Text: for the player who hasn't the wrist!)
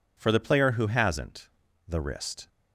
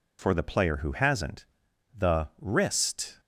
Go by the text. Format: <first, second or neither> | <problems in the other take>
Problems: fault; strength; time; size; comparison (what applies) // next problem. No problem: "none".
neither | pauses between "hasn't" and "the"; the same in both